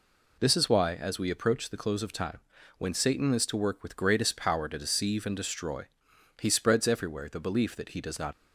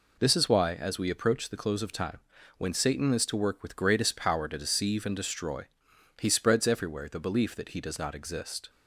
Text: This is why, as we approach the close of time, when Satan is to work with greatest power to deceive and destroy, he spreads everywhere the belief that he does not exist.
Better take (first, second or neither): second